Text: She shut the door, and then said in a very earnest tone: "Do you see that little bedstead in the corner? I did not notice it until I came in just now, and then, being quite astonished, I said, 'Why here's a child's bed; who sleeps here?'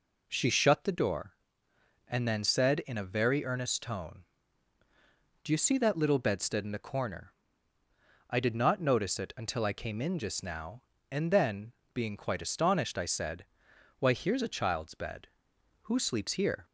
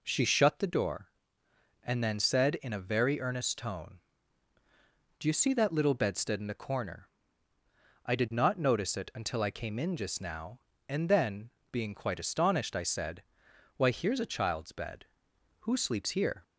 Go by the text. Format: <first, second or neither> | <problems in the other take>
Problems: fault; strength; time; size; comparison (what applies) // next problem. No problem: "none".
neither | none